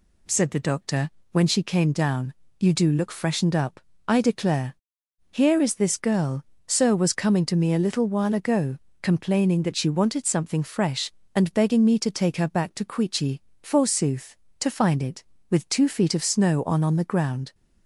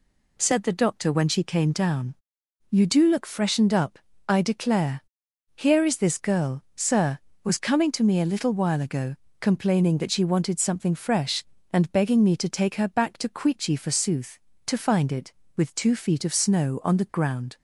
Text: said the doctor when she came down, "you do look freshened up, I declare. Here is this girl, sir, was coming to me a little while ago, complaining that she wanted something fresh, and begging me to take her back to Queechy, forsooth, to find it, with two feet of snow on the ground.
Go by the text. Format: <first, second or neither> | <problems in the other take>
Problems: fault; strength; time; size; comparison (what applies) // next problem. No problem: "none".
second | pauses between "doctor" and "when"; slight; at 1.0 s; 0.22 s long // says "on" twice; at 16.8 s